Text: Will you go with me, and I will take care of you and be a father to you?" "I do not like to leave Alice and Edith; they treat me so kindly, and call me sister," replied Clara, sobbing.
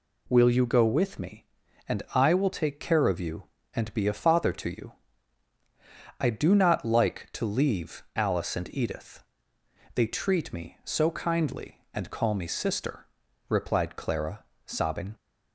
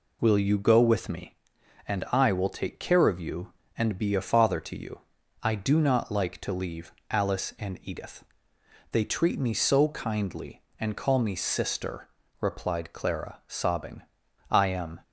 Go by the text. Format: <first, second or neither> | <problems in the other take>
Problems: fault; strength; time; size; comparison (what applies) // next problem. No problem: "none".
first | pauses between "leave" and "Alice"; slight; at 6.9 s; 0.18 s long // goes on to say "I am"; from 14.5 s on; 0.50 s long